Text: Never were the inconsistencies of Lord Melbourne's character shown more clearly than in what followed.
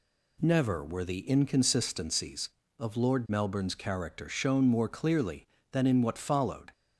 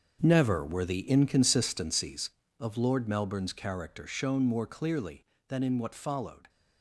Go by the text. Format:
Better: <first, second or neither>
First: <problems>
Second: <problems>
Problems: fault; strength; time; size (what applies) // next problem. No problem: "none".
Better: first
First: none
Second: gets quieter; strong; throughout; 12 dB